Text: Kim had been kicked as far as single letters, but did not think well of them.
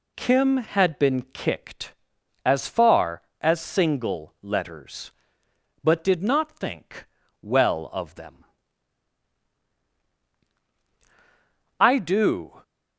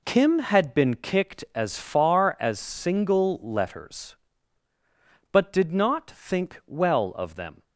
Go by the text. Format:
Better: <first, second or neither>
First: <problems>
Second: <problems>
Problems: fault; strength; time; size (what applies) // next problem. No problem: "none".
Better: second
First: pauses between "think" and "well"; slight; at 7.0 s; 0.36 s long // goes on to say "I do"; noticeable; from 11.8 s on; 0.82 s long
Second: none